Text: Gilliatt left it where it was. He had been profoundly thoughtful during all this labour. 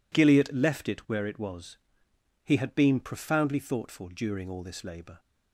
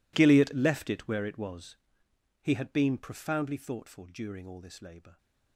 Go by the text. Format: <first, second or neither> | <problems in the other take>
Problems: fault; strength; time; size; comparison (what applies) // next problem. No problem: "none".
first | gets quieter; strong; throughout; 19 dB